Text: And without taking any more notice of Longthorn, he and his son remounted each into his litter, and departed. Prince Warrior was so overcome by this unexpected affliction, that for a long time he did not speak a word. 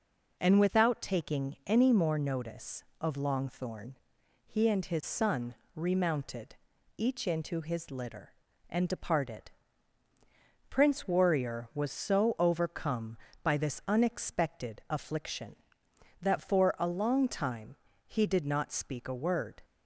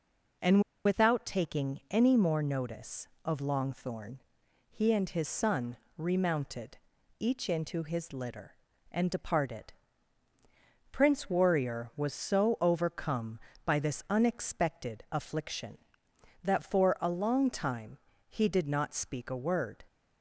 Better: first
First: pauses between "son" and "remounted"; slight; at 5.5 s; 0.20 s long // pauses between "remounted" and "each"; at 6.5 s; 0.42 s long // pauses between "time" and "he"; slight; at 17.7 s; 0.32 s long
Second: pauses between "And" and "without"; slight; at 0.6 s; 0.24 s long // pauses between "son" and "remounted"; slight; at 5.7 s; 0.20 s long // pauses between "remounted" and "each"; at 6.7 s; 0.42 s long // pauses between "time" and "he"; slight; at 17.9 s; 0.32 s long

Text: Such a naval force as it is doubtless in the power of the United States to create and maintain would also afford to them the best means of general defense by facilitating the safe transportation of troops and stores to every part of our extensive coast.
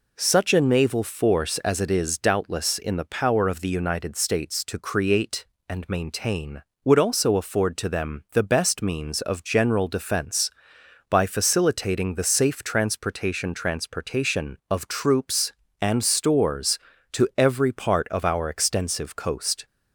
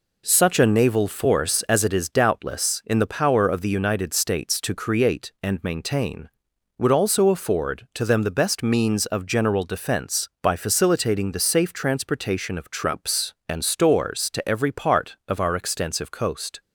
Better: second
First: says "transportation" twice; at 13.5 s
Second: none

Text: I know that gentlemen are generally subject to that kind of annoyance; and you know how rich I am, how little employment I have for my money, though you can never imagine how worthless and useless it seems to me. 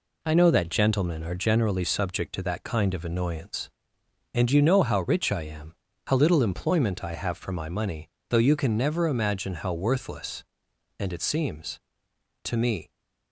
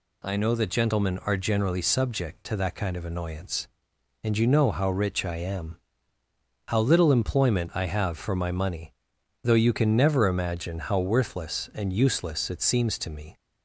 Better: second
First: skips "useless"; at 11.1 s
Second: none

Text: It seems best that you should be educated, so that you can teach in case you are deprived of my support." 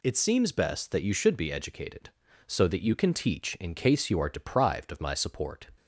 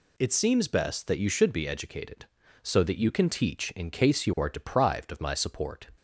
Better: neither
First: none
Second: none

